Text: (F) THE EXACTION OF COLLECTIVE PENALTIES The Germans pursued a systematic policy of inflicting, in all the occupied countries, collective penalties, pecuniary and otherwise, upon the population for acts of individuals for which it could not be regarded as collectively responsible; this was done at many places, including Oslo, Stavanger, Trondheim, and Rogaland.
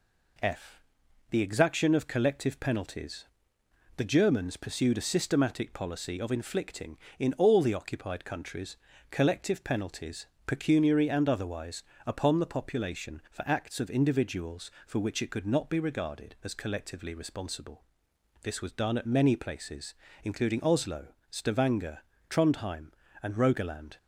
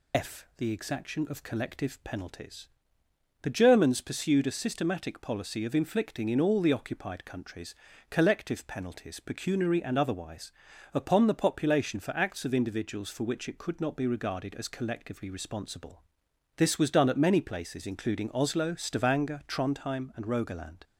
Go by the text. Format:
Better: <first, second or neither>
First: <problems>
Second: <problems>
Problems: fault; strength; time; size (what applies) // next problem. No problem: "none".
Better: first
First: pauses between "PENALTIES" and "The"; noticeable; at 3.2 s; 0.70 s long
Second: loses the start of "F"; at 0.1 s; 115 ms // pauses between "PENALTIES" and "The"; noticeable; at 2.6 s; 0.76 s long